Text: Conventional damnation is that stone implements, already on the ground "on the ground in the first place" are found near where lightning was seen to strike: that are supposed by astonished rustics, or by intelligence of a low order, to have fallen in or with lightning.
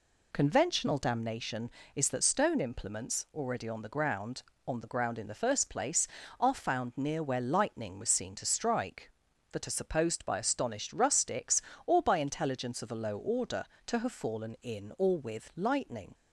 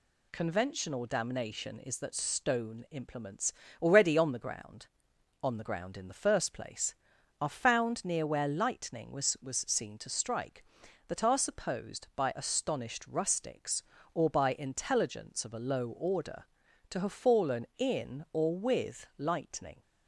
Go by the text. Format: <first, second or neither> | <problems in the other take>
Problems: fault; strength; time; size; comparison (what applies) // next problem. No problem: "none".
first | says "was" twice; at 9.4 s